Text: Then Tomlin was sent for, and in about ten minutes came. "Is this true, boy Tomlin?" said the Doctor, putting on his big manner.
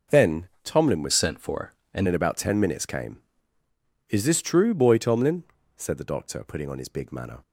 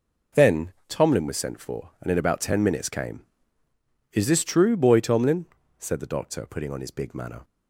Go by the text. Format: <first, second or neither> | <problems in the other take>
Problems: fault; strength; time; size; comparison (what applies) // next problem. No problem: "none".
second | pauses between "Then" and "Tomlin"; slight; at 0.4 s; 0.16 s long; slight in the second // changes voice from "sent" to "and"; from 1.1 to 2.0 s; 0.9 s long